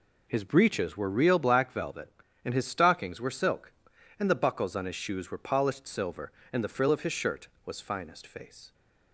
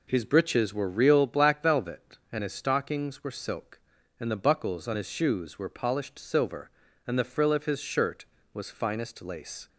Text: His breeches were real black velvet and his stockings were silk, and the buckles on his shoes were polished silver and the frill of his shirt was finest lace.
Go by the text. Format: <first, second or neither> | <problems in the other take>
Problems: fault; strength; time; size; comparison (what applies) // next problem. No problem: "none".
second | says "face" for "lace"; at 8.2 s